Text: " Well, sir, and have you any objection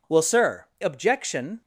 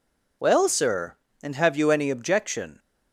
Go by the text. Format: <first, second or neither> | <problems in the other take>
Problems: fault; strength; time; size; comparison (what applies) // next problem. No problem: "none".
second | skips "and have you any"; at 0.7 s